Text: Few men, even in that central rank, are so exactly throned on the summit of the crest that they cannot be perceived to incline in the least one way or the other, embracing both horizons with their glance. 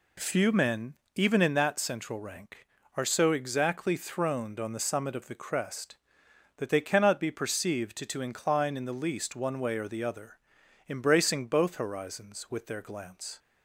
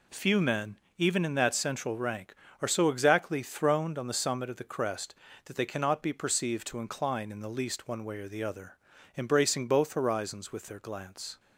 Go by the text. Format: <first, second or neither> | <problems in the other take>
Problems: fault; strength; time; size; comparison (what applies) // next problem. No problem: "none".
second | says "to" twice; at 8.0 s